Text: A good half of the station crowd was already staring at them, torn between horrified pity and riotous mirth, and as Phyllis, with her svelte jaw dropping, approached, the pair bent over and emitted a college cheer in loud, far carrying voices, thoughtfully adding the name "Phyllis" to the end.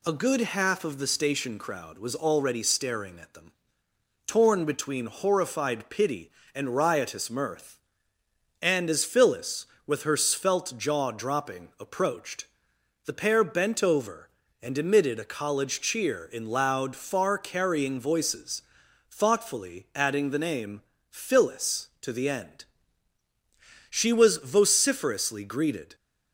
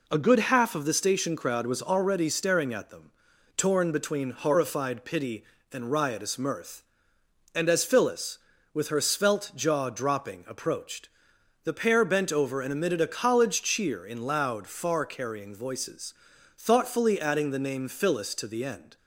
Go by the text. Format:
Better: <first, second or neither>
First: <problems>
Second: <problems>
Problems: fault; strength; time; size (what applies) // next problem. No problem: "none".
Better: second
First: pauses between "name" and "Phyllis"; slight; at 20.8 s; 0.30 s long // goes on to say "She was vociferously greeted"; strong; from 23.8 s on; 2.0 s long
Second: none